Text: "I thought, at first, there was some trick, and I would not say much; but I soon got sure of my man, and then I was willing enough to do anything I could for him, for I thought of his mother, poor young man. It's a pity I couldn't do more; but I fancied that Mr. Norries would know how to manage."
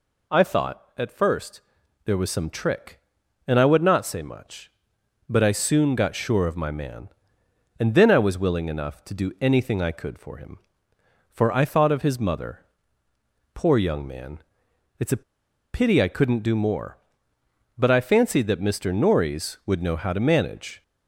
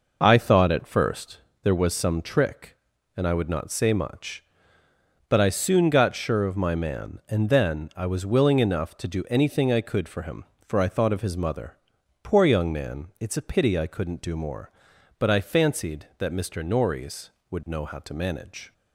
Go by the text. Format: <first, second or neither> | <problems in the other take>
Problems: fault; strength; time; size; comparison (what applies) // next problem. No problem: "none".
second | pauses between "a" and "pity"; noticeable; at 15.2 s; 0.52 s long